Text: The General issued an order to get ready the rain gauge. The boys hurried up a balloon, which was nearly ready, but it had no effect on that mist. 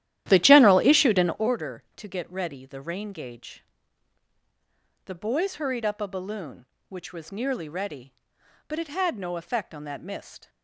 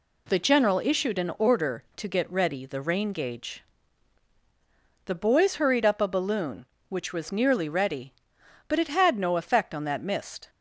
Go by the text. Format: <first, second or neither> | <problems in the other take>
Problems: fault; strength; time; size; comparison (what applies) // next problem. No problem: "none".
second | starts louder than the rest; strong; until 1.5 s; 12.5 dB